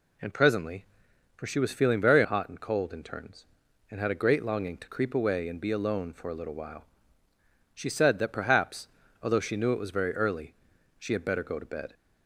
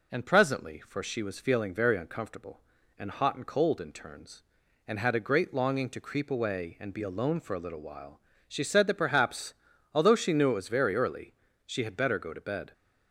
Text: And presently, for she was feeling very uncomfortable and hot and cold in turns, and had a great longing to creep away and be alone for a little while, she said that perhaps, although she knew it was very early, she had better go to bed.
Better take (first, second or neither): second